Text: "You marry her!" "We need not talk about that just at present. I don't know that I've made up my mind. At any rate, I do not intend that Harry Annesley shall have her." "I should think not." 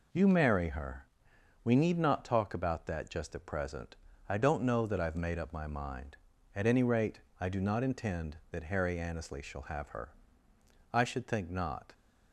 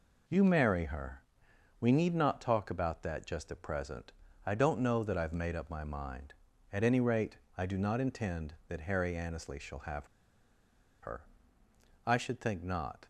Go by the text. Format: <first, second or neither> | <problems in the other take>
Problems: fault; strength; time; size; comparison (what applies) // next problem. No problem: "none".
first | pauses between "have" and "her"; noticeable; at 10.0 s; 0.95 s long